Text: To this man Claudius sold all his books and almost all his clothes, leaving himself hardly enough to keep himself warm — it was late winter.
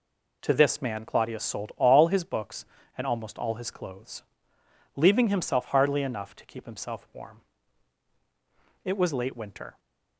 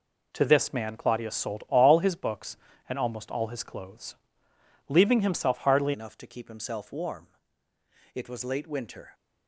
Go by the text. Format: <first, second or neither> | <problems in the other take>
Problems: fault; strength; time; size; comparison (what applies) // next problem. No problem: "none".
first | changes voice at "enough"; from 5.9 s on; 3.2 s long